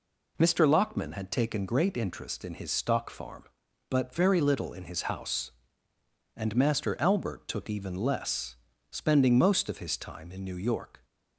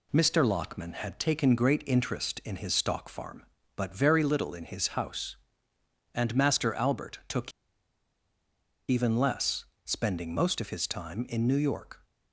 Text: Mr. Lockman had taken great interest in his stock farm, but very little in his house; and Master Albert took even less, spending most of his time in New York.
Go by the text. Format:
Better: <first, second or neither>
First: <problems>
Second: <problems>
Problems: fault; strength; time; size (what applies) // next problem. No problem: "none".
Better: first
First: none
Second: pauses between "took" and "even"; strong; at 7.5 s; 1.3 s long